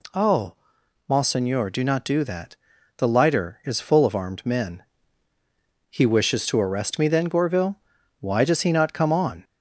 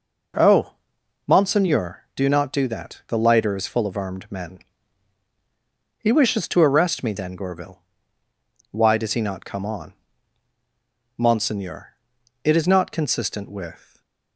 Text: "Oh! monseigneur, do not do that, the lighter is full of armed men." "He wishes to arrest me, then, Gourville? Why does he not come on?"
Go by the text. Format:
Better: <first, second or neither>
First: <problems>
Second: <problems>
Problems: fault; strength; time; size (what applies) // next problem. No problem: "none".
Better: first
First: none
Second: goes on to say "Monseigneur it is not consistent with"; strong; from 11.1 s on; 2.8 s long // stays silent after the last word; slight; from 13.8 s on; 0.5 s long